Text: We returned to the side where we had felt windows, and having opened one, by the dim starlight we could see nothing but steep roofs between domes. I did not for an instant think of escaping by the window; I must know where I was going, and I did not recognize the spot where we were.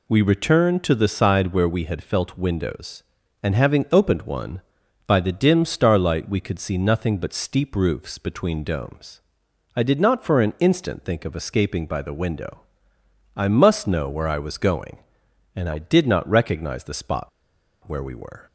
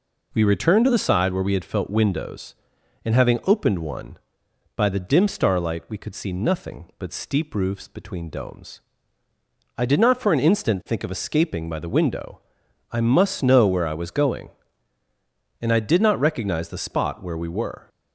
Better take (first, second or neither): second